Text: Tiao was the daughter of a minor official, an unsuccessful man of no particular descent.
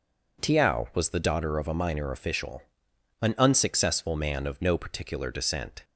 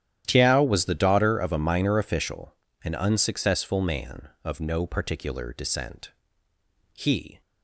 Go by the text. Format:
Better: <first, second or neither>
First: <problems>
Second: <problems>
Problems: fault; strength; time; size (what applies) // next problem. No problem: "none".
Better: first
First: none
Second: starts louder than the rest; strong; until 1.2 s; 11 dB // goes on to say "He"; slight; from 6.9 s on; 0.48 s long